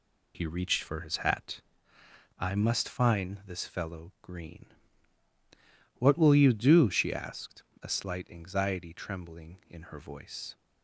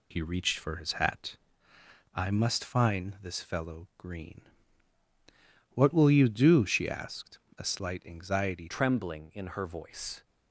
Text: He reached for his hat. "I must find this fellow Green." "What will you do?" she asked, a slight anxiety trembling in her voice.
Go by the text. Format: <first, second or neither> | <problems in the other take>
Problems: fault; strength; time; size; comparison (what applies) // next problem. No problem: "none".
first | changes voice at "trembling"; from 8.6 s on; 1.6 s long